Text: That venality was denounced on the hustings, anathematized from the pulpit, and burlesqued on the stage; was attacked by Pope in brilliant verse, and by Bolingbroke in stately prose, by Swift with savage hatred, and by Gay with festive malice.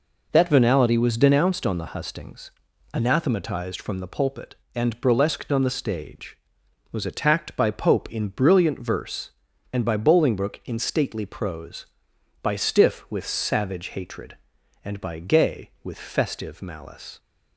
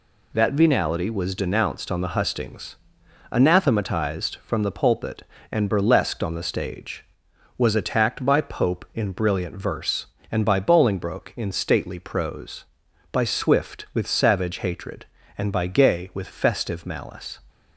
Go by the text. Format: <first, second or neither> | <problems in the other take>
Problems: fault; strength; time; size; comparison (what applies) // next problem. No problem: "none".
second | says "Stiff" for "Swift"; at 12.5 s